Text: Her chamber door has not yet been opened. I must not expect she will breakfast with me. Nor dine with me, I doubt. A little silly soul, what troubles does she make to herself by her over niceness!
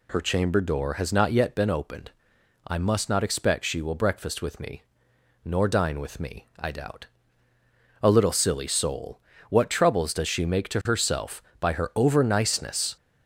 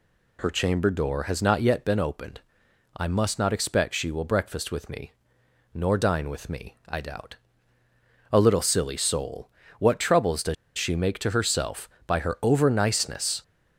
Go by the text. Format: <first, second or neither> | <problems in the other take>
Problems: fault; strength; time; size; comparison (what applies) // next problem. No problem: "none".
first | pauses between "does" and "she"; slight; at 10.5 s; 0.23 s long